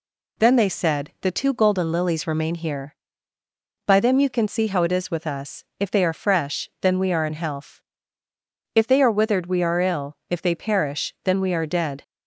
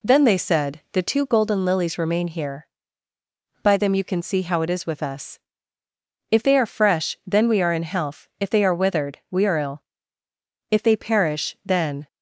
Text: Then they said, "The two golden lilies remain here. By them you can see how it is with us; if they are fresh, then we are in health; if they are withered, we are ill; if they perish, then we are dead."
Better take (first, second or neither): first